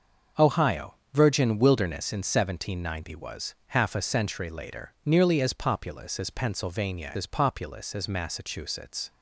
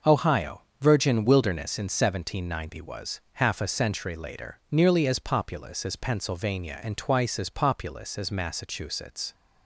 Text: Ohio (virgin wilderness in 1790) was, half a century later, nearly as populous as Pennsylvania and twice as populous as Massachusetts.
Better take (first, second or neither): second